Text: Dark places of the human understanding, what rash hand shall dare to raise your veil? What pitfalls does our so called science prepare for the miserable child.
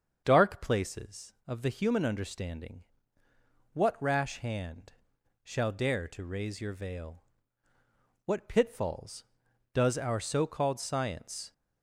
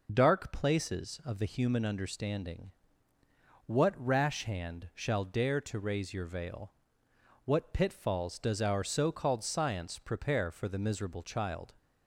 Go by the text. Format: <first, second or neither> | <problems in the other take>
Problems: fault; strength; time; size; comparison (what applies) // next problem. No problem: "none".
second | starts louder than the rest; until 1.2 s; 7 dB // pauses between "hand" and "shall"; noticeable; at 4.9 s; 0.50 s long // stops before "prepare for the miserable child"; at 11.5 s